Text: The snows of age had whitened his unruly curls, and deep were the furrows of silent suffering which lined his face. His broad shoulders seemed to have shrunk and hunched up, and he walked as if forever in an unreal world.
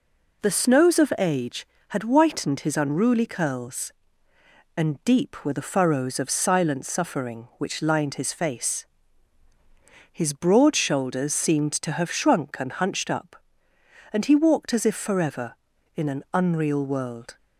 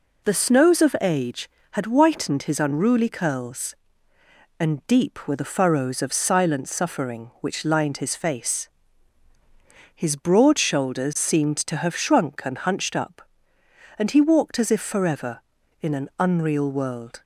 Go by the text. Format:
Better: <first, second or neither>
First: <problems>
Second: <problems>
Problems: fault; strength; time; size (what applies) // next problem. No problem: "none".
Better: neither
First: none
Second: none